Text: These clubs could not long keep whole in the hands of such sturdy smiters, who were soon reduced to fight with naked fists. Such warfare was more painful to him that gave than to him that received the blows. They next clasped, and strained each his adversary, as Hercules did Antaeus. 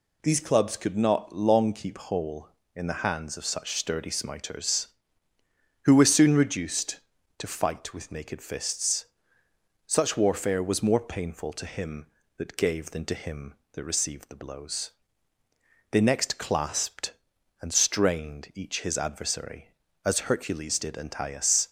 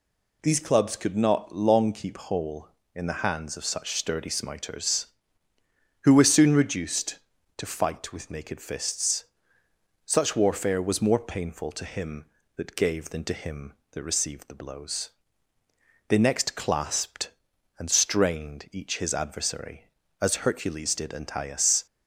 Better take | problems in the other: neither | none

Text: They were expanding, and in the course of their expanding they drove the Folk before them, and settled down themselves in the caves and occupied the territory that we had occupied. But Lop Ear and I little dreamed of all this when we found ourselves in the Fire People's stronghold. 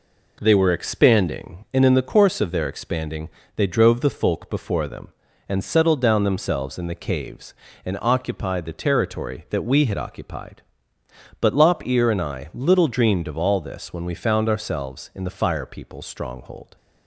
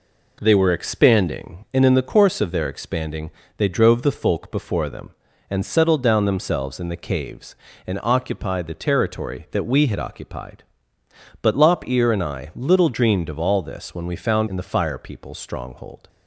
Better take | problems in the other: first | pauses between "expanding" and "they"; slight; at 3.2 s; 0.28 s long; slight in the first // skips "ourselves"; at 14.4 s

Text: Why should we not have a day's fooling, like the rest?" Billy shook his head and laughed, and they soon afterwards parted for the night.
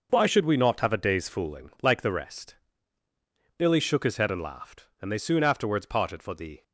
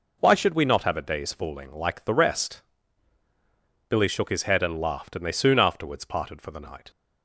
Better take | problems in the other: second | stops before "night"; at 6.6 s

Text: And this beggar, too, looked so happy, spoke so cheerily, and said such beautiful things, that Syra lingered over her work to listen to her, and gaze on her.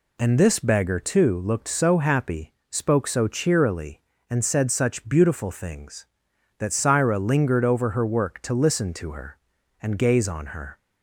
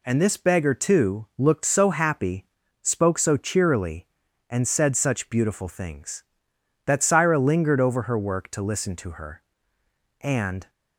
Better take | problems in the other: first | stops before "gaze on her"; at 10.6 s

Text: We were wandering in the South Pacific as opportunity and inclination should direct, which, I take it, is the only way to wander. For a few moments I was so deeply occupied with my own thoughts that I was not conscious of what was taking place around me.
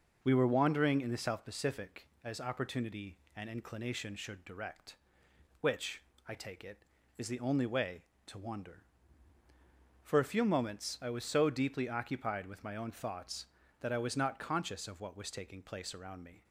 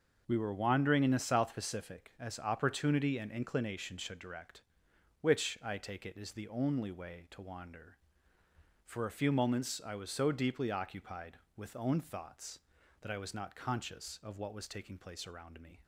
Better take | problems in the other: first | starts louder than the rest; noticeable; until 1.2 s; 6 dB // skips "my"; at 11.7 s

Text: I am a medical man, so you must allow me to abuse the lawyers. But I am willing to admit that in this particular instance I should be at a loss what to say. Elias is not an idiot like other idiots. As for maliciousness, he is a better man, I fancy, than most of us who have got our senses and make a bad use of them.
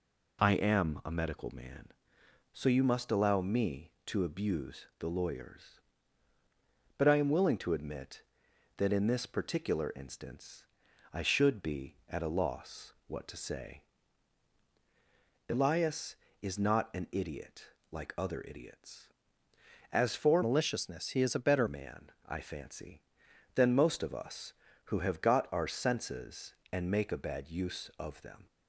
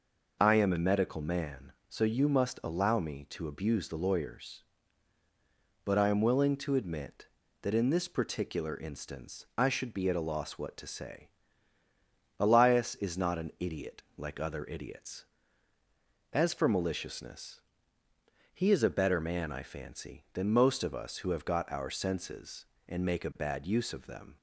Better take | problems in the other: second | pauses between "instance" and "I"; noticeable; at 10.6 s; 0.48 s long // pauses between "idiot" and "like"; slight; at 17.6 s; 0.26 s long // changes voice from "maliciousness" to "better"; from 20.4 to 21.6 s; 1.2 s long

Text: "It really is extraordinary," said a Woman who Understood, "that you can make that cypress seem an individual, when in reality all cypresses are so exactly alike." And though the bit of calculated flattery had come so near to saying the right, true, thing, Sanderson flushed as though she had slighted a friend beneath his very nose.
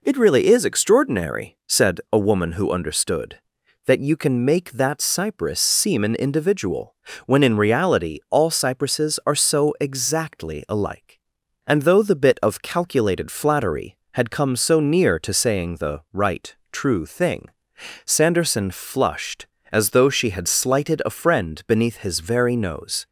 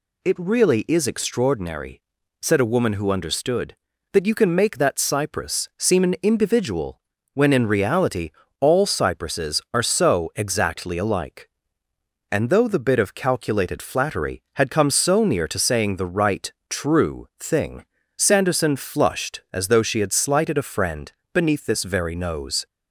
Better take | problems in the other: first | pauses between "reality" and "all"; slight; at 8.2 s; 0.30 s long // pauses between "friend" and "beneath"; slight; at 21.1 s; 0.20 s long // says "this" for "his"; at 21.6 s

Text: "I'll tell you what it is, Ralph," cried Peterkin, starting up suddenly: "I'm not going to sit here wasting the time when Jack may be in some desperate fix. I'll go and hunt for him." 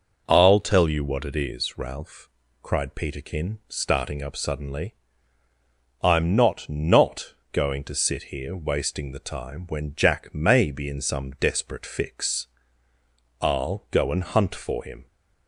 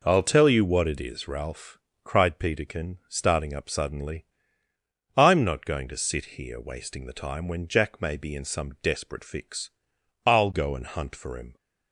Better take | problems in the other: second | says "not" twice; at 6.6 s

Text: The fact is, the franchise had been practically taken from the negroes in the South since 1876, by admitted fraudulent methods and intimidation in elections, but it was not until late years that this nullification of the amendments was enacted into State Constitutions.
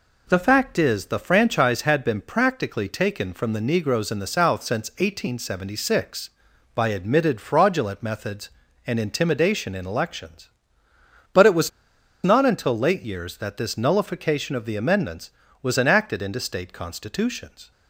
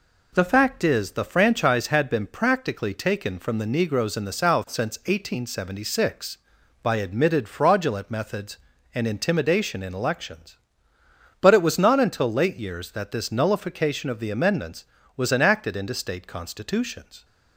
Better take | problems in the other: second | pauses between "was" and "not"; noticeable; at 11.6 s; 0.54 s long

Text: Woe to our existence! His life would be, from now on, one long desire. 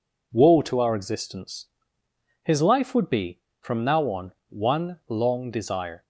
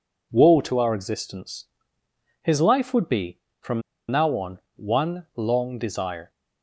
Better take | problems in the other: first | pauses between "from" and "now"; slight; at 3.8 s; 0.28 s long

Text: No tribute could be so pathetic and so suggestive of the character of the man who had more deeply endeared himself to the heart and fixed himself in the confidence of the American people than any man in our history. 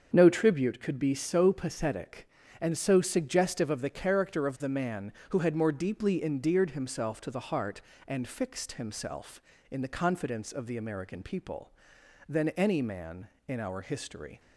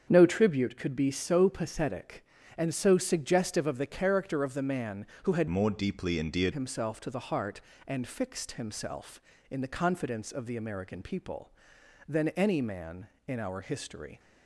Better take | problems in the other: first | starts louder than the rest; strong; until 1.0 s; 7 dB; also in the first // changes voice from "more" to "endeared"; from 5.4 to 6.5 s; 1.1 s long

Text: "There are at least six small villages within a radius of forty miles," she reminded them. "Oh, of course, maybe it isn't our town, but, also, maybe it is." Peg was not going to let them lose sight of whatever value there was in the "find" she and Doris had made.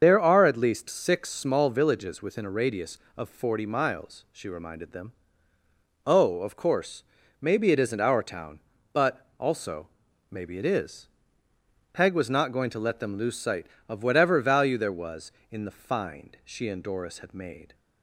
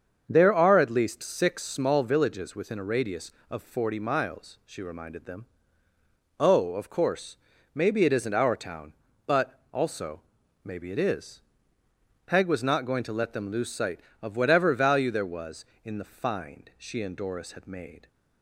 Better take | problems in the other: second | loses the start of "There"; at 0.0 s; 75 ms // starts louder than the rest; until 1.0 s; 7 dB; also in the second

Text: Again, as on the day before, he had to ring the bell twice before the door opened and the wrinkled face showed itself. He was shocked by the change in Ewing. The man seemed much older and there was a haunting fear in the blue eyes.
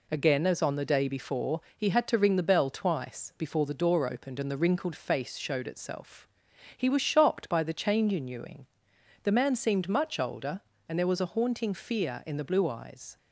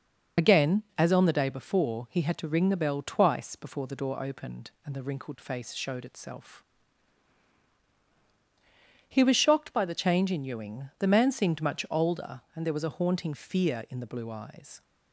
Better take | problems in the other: first | loses the start of "Again"; at 0.3 s; 35 ms

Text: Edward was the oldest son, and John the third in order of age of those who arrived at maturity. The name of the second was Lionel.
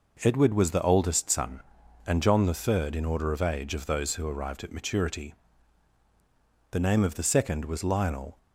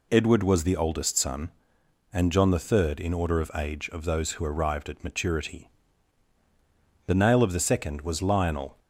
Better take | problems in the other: first | says "nail" for "name"; at 7.1 s

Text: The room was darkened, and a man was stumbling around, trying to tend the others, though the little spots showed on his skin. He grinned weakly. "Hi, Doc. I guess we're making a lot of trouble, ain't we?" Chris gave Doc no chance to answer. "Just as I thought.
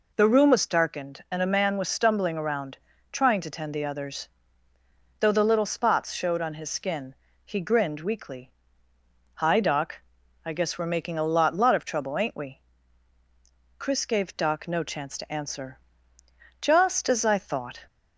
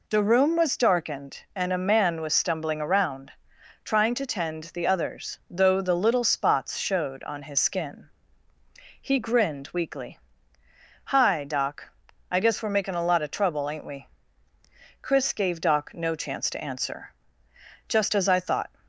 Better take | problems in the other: second | says "lot" twice; at 11.5 s

